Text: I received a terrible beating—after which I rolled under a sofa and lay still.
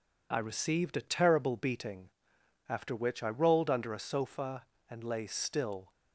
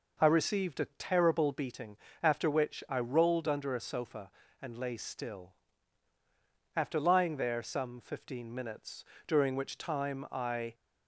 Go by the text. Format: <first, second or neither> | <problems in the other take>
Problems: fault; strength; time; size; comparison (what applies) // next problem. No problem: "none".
first | goes on to say "After lying there some fifteen minutes during which time I"; strong; from 6.7 s on; 4.0 s long